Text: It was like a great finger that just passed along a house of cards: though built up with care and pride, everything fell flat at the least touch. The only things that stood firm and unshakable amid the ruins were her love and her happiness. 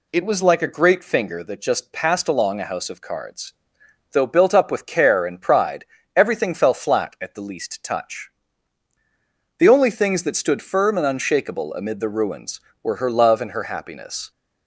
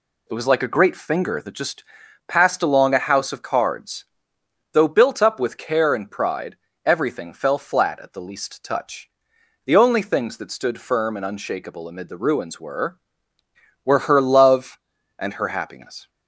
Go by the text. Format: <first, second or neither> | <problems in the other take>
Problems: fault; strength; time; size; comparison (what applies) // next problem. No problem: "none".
first | pauses between "just" and "passed"; at 1.8 s; 0.44 s long // says "were" twice; at 13.8 s